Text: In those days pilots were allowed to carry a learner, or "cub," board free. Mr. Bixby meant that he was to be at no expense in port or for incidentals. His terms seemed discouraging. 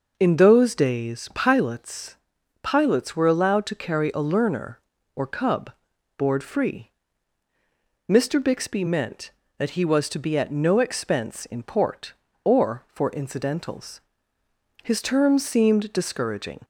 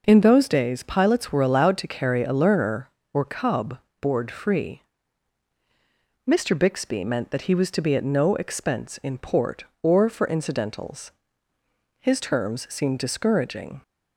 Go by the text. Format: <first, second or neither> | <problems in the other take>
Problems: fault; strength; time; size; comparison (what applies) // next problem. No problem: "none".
second | says "pilots" twice; at 2.6 s